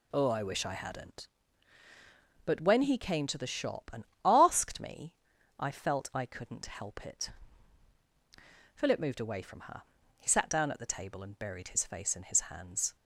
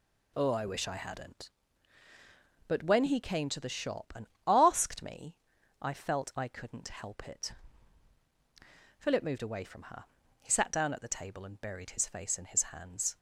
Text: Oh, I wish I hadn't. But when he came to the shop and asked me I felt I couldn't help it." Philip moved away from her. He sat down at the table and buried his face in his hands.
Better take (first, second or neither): neither